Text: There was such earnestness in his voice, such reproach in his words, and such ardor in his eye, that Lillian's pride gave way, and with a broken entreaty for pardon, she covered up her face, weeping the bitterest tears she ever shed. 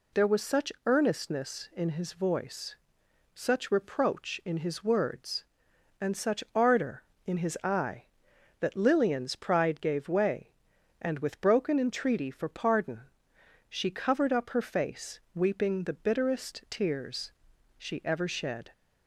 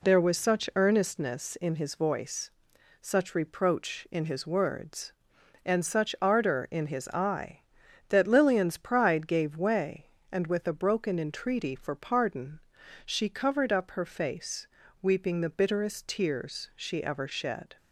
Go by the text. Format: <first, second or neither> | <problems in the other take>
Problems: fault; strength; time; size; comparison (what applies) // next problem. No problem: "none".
second | skips "a"; at 11.4 s // pauses between "tears" and "she"; noticeable; at 17.3 s; 0.48 s long